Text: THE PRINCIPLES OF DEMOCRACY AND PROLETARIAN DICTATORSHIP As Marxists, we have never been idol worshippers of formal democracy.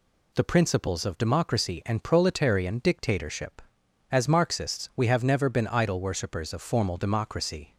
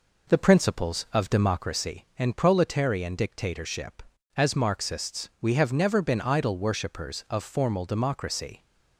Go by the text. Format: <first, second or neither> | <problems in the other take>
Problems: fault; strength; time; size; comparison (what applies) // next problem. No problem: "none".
first | starts louder than the rest; noticeable; until 1.7 s; 4.5 dB